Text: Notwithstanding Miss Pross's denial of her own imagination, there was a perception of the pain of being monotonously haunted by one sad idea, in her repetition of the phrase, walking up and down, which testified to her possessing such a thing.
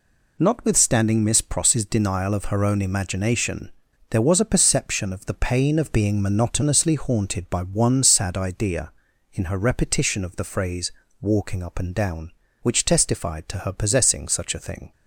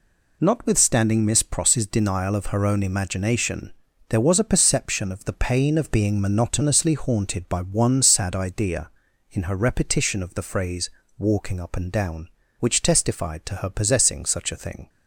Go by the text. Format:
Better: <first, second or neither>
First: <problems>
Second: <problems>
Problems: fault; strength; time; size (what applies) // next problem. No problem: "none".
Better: neither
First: none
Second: none